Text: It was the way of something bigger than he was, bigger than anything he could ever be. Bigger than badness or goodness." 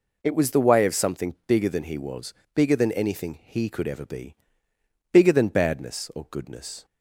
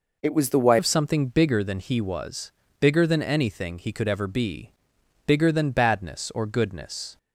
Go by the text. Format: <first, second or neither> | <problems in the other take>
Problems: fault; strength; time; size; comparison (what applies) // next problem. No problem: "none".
first | changes voice at "of"; from 0.7 s on; 6.4 s long